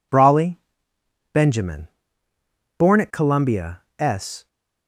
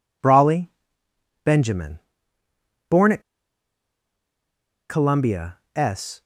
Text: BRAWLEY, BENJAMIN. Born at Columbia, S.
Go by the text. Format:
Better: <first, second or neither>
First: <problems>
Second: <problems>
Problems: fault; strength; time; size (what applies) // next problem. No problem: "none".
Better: first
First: none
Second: pauses between "at" and "Columbia"; strong; at 3.2 s; 1.6 s long